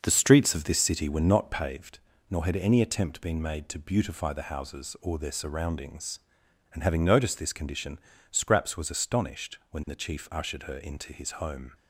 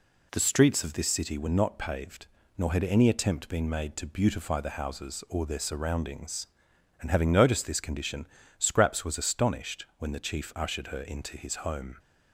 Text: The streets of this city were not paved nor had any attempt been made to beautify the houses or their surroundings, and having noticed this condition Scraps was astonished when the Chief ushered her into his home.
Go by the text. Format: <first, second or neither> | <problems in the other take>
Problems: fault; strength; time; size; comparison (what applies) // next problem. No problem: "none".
second | starts louder than the rest; until 1.8 s; 6.5 dB // pauses between "paved" and "nor"; slight; at 1.9 s; 0.34 s long; slight in the second // pauses between "condition" and "Scraps"; slight; at 7.9 s; 0.32 s long; slight in the second